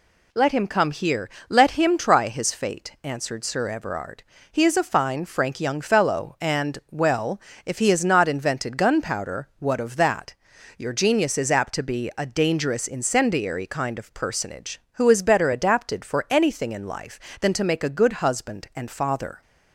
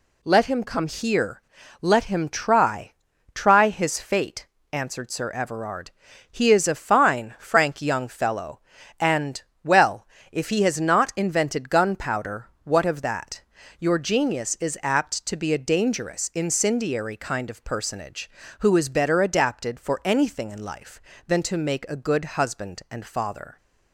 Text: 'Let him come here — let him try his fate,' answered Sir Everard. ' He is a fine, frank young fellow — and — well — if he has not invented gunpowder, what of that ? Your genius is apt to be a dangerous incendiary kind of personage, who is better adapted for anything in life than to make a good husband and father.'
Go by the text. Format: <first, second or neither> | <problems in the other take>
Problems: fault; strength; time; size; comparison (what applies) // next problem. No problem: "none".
first | says "try" twice; at 3.3 s